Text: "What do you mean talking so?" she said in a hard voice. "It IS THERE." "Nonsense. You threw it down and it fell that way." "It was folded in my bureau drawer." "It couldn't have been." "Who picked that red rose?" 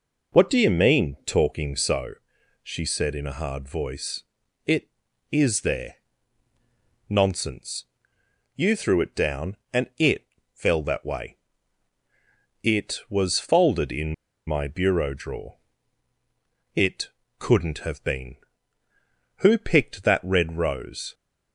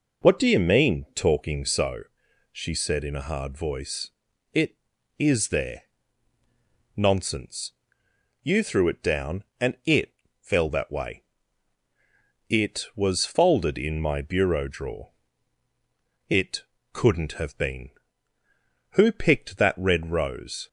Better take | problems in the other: second | pauses between "it" and "fell"; slight; at 10.2 s; 0.26 s long; slight in the second // pauses between "in" and "my"; slight; at 14.1 s; 0.33 s long // pauses between "It" and "couldn't"; slight; at 17.0 s; 0.28 s long; slight in the second

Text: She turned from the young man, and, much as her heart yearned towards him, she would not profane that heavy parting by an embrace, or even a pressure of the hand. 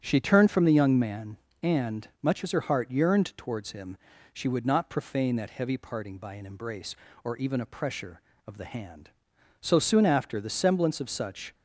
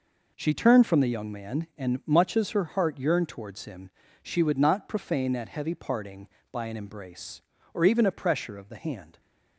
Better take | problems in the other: second | starts louder than the rest; strong; until 1.0 s; 8.5 dB // goes on to say "So soon after the semblance of such"; strong; from 9.5 s on; 1.9 s long

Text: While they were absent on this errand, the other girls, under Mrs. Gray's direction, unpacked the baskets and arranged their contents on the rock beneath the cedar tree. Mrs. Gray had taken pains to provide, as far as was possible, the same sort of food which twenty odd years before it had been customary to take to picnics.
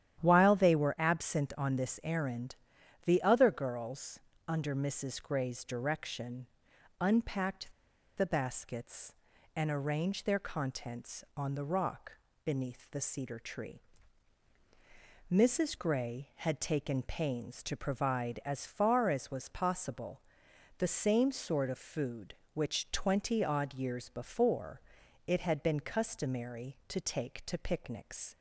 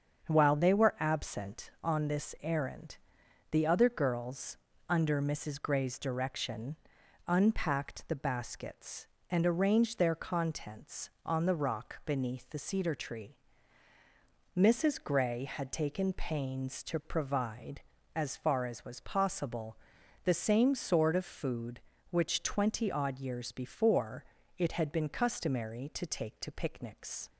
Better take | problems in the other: second | starts louder than the rest; strong; until 1.2 s; 10.5 dB; strong in the second // pauses between "unpacked" and "the"; at 7.7 s; 0.45 s long // pauses between "rock" and "beneath"; slight; at 12.1 s; 0.32 s long // pauses between "before" and "it"; noticeable; at 24.8 s; 0.46 s long; slight in the second

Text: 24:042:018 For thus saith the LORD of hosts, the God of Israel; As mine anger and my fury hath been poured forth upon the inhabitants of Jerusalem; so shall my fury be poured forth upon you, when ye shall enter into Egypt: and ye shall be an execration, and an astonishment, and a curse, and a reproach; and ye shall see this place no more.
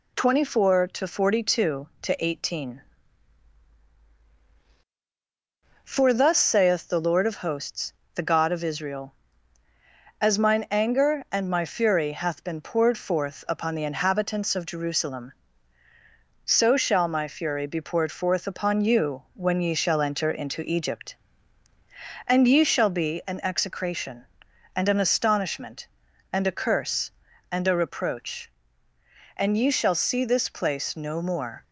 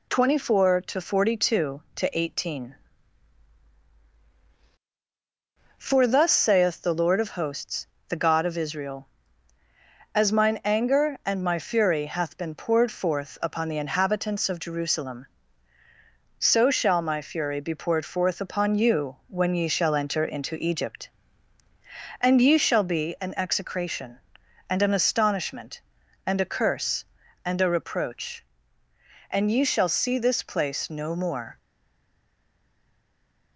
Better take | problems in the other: first | stays silent after the last word; noticeable; from 31.5 s on; 2.0 s long

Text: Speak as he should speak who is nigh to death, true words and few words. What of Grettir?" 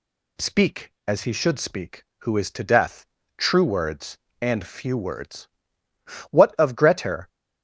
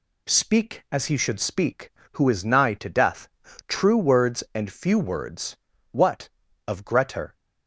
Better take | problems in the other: second | skips "nigh"; at 2.5 s

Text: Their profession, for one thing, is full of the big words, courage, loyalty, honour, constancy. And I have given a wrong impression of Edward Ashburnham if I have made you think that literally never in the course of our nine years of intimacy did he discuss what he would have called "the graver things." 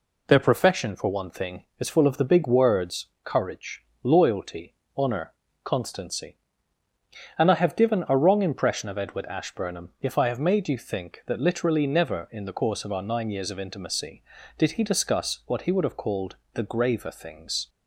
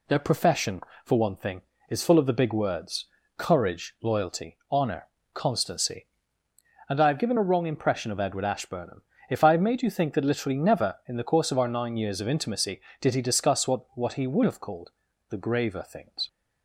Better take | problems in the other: first | pauses between "Ashburnham" and "if"; slight; at 9.0 s; 0.26 s long // says "what" twice; at 13.9 s // pauses between "called" and "the"; at 14.9 s; 0.38 s long; slight in the first

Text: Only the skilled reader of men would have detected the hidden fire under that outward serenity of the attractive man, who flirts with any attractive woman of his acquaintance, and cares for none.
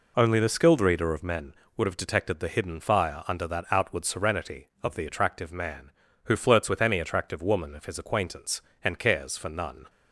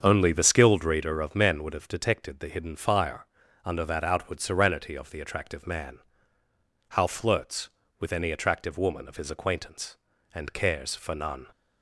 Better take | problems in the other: first | starts louder than the rest; until 1.0 s; 7 dB // pauses between "fire" and "under"; at 3.2 s; 0.38 s long // says "how" for "who"; at 6.8 s

